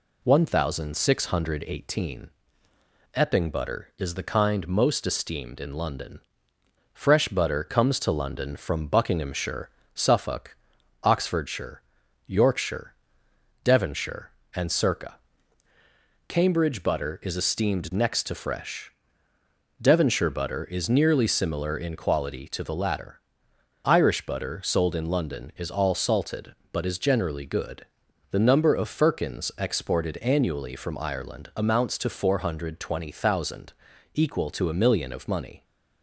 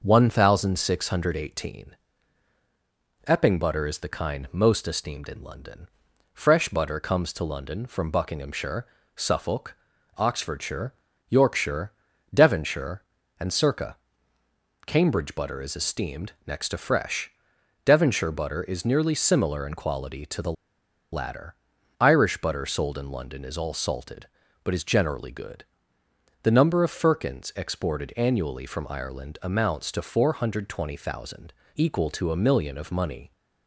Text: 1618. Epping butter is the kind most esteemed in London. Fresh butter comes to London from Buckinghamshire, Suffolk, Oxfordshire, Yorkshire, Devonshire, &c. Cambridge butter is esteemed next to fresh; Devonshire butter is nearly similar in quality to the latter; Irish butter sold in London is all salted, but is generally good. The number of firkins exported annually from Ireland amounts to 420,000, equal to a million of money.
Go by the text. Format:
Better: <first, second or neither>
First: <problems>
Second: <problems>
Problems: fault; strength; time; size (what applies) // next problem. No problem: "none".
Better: first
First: none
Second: pauses between "esteemed" and "next"; slight; at 16.3 s; 0.16 s long // pauses between "the" and "latter"; noticeable; at 20.5 s; 0.60 s long